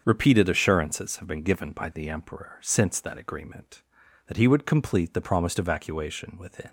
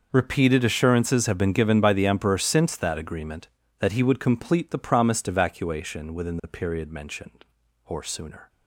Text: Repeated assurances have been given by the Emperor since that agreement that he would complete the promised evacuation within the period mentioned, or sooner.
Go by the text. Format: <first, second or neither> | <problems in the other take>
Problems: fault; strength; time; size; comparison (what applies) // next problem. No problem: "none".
second | starts louder than the rest; until 1.0 s; 7 dB // stops before "the period mentioned or sooner"; at 6.6 s